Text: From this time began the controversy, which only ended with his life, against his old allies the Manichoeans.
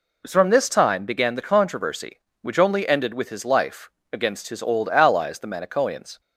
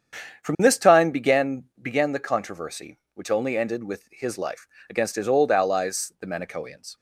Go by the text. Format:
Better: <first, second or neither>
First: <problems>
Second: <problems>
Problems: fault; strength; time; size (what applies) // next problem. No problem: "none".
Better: first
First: none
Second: starts louder than the rest; strong; until 1.4 s; 8 dB // says "began" twice; at 1.8 s